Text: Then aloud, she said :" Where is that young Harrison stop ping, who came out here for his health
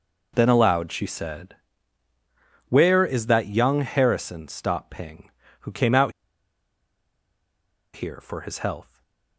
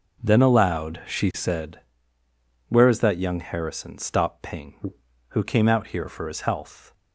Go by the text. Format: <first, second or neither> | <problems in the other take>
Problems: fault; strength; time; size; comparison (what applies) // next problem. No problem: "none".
second | pauses between "out" and "here"; strong; at 6.1 s; 1.8 s long // stays silent after the last word; slight; from 8.8 s on; 0.5 s long